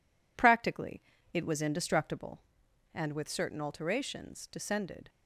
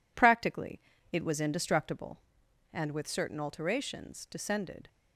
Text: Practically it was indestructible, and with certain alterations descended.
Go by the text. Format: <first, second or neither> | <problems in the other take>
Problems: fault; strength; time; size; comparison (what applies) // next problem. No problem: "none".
neither | pauses between "Practically" and "it"; slight; the same in both